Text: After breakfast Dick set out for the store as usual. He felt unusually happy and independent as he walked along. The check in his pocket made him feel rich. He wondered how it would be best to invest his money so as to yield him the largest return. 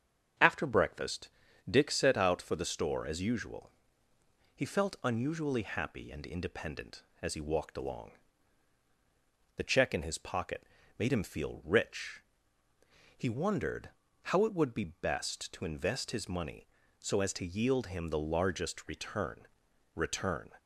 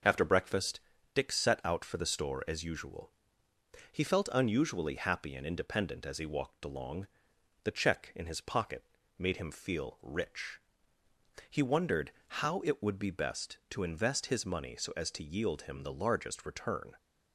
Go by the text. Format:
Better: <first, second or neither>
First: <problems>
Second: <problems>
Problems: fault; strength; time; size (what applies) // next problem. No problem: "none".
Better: second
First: starts louder than the rest; strong; until 1.7 s; 8 dB // pauses between "breakfast" and "Dick"; at 1.2 s; 0.40 s long // pauses between "pocket" and "made"; slight; at 10.6 s; 0.32 s long // pauses between "wondered" and "how"; slight; at 13.8 s; 0.34 s long // says "return" twice; at 19.9 s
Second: starts louder than the rest; noticeable; until 1.4 s; 6 dB // pauses between "breakfast" and "Dick"; slight; at 0.7 s; 0.34 s long // pauses between "pocket" and "made"; slight; at 8.8 s; 0.34 s long // pauses between "wondered" and "how"; slight; at 12.1 s; 0.16 s long